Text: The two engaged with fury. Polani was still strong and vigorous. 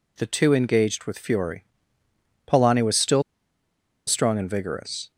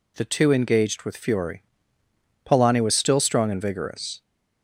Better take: second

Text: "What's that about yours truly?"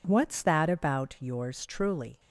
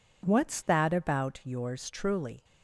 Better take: neither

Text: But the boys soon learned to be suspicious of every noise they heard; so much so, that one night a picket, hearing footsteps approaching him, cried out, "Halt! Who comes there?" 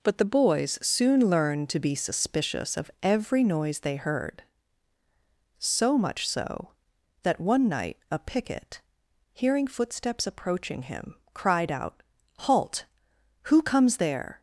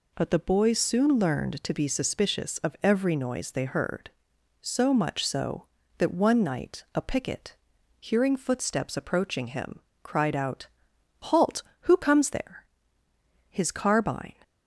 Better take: first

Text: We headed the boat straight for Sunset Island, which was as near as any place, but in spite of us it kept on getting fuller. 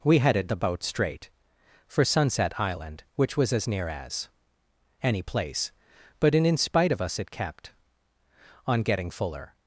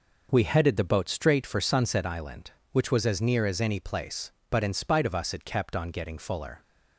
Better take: second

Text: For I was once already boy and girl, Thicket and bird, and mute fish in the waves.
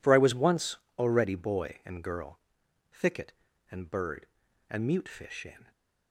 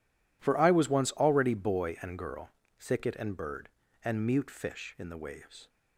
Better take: second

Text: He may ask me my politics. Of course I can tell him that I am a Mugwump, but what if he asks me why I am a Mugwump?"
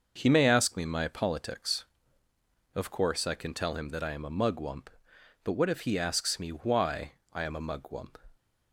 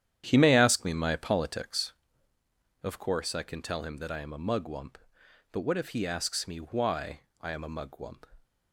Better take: first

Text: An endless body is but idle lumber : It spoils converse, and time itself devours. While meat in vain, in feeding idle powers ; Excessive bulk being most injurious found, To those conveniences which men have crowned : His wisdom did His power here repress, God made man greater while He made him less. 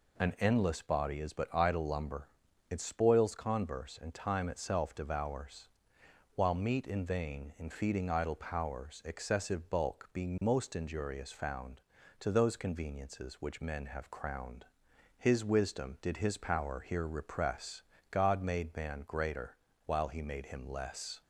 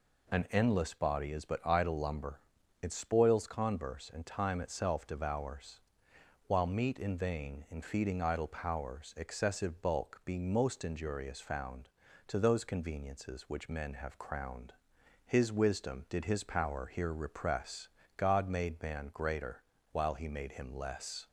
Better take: neither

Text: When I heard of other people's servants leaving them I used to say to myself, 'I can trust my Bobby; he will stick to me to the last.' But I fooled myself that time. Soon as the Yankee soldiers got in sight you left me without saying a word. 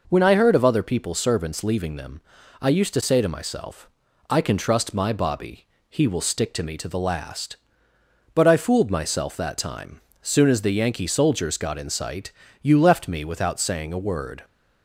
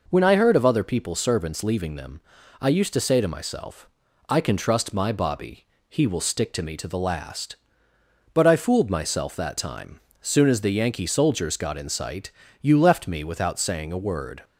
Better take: neither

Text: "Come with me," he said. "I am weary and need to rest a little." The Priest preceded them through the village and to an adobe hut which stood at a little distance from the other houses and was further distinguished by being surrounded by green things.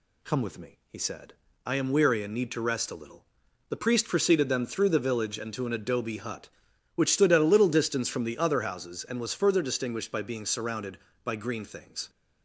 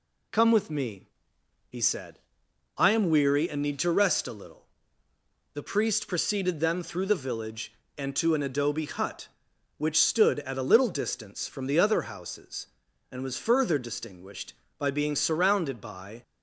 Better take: first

